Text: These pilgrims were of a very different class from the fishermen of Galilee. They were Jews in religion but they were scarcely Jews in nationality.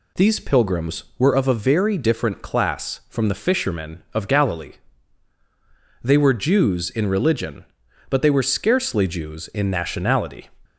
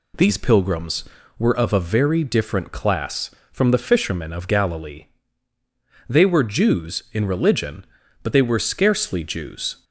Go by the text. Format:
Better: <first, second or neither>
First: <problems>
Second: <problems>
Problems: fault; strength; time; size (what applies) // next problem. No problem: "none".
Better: first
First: none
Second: stops before "in nationality"; at 9.8 s